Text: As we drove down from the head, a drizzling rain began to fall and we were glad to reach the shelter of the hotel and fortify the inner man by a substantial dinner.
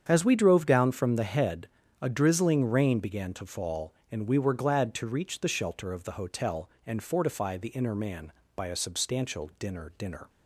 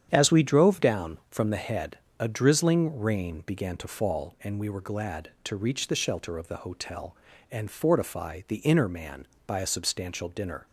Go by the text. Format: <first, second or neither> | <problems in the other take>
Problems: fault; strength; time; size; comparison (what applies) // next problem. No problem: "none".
second | starts louder than the rest; strong; until 1.0 s; 8 dB; strong in the second // says "dinner" twice; at 9.9 s